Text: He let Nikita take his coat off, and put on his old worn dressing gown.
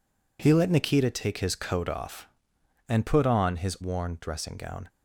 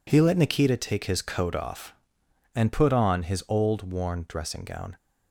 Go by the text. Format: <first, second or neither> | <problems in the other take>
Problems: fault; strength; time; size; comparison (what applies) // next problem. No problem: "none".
second | skips "old"; at 3.7 s